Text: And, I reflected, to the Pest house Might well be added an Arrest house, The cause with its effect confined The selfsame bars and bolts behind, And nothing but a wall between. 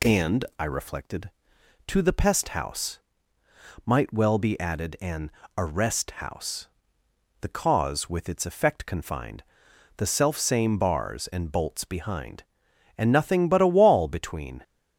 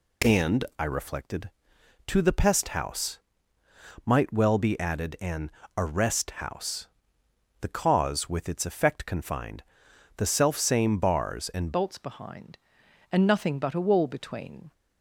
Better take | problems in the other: first | pauses between "house" and "Might"; noticeable; at 3.1 s; 0.86 s long; noticeable in the first // pauses between "an" and "Arrest"; slight; at 5.5 s; 0.26 s long; slight in the first // pauses between "confined" and "The"; noticeable; at 9.6 s; 0.54 s long; noticeable in the first // changes voice at "bolts"; from 11.7 s on; 3.0 s long

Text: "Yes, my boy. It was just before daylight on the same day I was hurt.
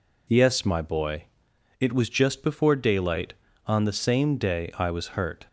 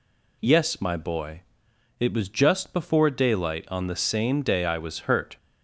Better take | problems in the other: neither | none

